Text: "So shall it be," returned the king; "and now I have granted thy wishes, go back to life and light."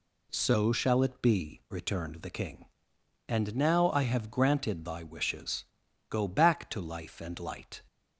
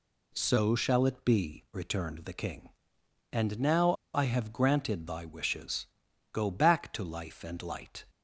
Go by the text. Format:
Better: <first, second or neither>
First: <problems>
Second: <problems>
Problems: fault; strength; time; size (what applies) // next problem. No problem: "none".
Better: first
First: none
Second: pauses between "now" and "I"; slight; at 3.9 s; 0.20 s long